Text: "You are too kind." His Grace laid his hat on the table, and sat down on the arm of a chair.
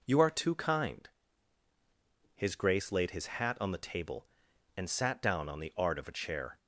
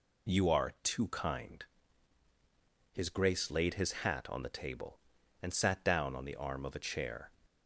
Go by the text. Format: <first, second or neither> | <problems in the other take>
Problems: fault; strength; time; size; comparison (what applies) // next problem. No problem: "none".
second | says "art" for "arm"; at 5.7 s